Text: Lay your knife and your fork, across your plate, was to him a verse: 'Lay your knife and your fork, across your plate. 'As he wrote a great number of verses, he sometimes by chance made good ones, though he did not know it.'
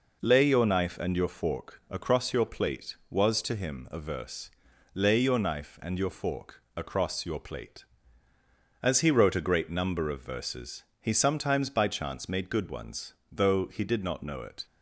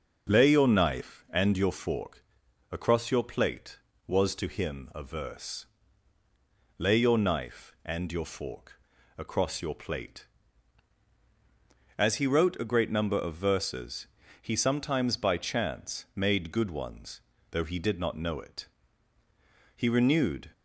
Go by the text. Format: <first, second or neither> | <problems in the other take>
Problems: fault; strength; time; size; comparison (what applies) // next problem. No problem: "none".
first | goes on to say "He renewed"; noticeable; from 19.7 s on; 0.76 s long